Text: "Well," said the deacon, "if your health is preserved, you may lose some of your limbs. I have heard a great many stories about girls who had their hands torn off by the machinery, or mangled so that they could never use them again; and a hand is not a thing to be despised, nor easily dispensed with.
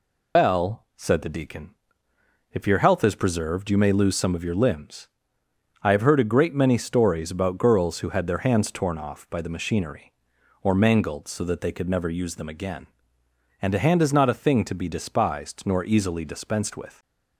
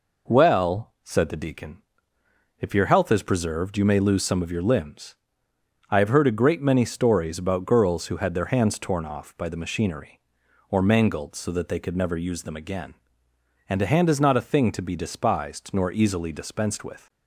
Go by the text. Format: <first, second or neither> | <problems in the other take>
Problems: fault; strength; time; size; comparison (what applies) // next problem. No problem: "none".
second | loses the start of "Well"; at 0.3 s; 150 ms